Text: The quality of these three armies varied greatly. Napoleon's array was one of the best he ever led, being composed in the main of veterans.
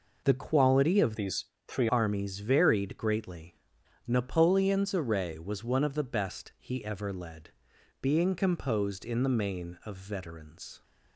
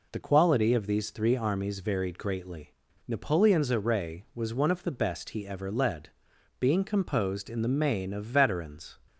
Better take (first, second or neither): second